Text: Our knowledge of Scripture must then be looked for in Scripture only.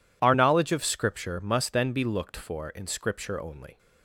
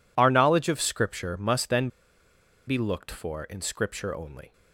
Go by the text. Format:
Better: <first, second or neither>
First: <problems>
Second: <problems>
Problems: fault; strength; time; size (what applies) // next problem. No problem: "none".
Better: first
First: none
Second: pauses between "then" and "be"; noticeable; at 1.8 s; 0.80 s long